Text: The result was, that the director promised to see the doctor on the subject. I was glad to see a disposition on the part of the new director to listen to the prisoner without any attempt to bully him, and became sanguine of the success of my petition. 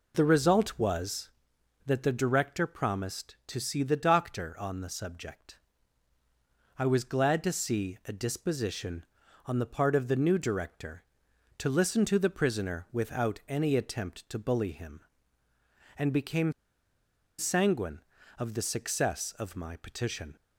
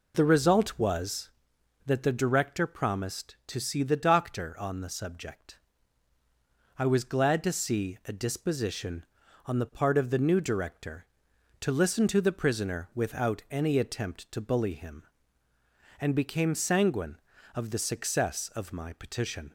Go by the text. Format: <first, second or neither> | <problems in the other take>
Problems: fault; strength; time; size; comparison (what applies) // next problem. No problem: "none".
second | pauses between "became" and "sanguine"; noticeable; at 16.5 s; 0.87 s long